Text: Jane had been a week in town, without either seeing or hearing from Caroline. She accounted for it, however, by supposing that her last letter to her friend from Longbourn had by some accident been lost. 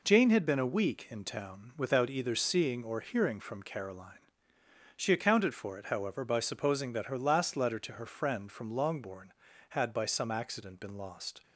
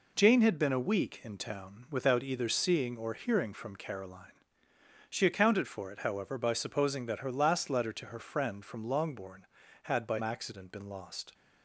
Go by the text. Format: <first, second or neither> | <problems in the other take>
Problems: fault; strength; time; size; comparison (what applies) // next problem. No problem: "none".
first | skips "some"; at 10.2 s